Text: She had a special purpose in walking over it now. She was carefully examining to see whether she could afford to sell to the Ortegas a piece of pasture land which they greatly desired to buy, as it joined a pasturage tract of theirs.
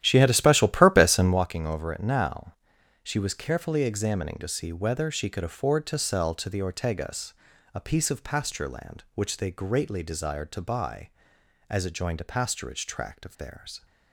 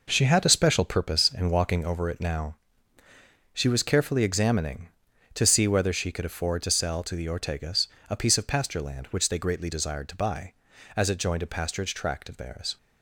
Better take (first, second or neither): second